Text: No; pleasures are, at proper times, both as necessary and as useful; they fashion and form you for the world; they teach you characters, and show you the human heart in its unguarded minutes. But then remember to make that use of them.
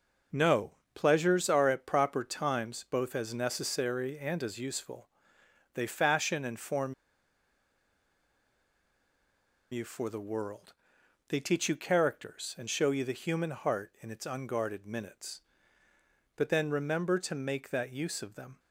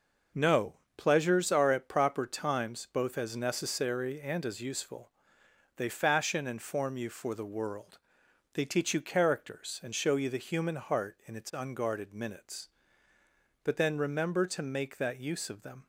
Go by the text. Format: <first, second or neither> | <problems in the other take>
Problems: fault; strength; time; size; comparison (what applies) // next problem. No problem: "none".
second | pauses between "form" and "you"; strong; at 6.9 s; 2.7 s long